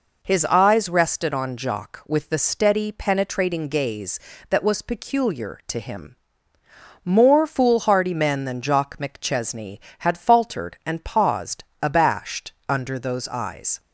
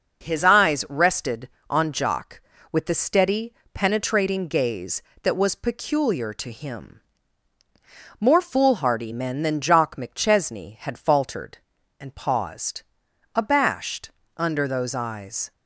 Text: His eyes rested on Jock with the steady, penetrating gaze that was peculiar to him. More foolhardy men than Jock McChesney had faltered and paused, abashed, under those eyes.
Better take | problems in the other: neither | none

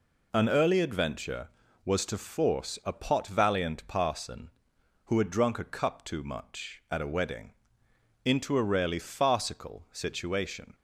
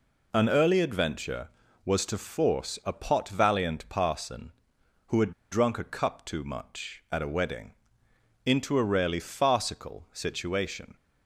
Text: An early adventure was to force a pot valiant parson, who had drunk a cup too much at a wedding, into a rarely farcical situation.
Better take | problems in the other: first | pauses between "had" and "drunk"; slight; at 5.3 s; 0.19 s long

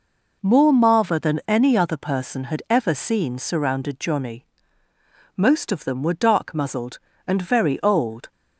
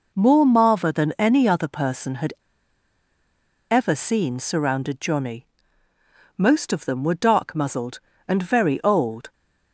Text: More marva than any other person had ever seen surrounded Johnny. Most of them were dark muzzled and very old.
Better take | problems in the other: first | pauses between "had" and "ever"; strong; at 2.3 s; 1.3 s long

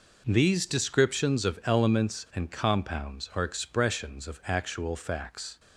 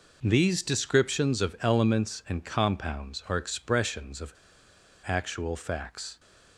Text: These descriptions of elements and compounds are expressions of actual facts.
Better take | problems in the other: first | pauses between "of" and "actual"; noticeable; at 4.3 s; 0.70 s long

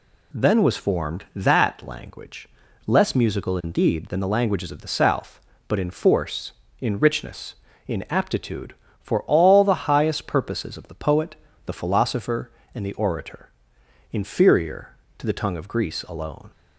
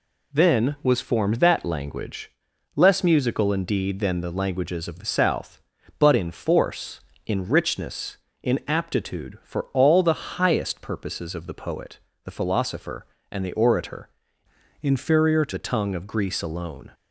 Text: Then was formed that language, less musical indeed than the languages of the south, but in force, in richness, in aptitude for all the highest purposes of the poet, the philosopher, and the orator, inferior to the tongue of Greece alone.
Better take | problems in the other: first | changes voice from "inferior" to "to"; from 14.8 to 15.5 s; 0.7 s long

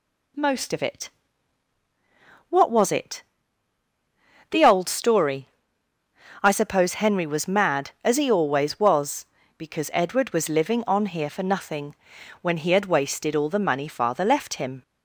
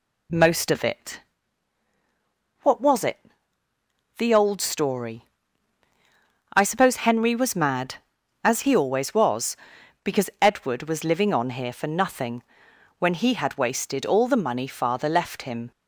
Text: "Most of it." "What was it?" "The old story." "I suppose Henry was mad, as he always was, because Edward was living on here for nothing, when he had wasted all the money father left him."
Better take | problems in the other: neither | none

